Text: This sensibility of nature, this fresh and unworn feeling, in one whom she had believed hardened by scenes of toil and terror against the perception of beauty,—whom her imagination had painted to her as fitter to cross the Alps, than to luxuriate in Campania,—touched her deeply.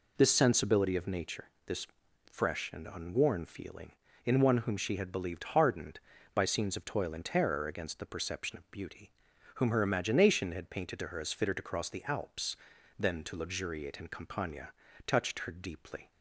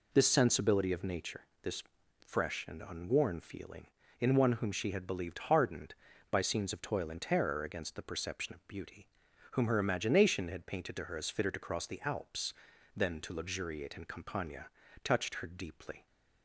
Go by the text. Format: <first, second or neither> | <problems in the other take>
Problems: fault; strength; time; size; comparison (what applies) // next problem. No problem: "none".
neither | pauses between "this" and "fresh"; the same in both